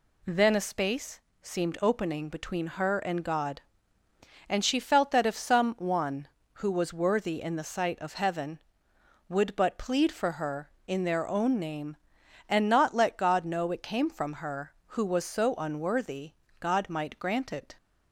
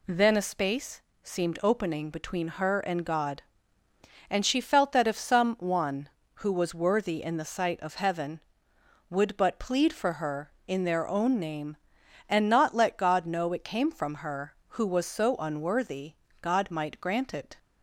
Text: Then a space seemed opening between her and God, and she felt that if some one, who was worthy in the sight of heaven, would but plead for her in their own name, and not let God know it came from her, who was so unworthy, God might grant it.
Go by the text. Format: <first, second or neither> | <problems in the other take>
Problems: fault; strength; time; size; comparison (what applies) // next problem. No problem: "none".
neither | pauses between "space" and "seemed"; slight; the same in both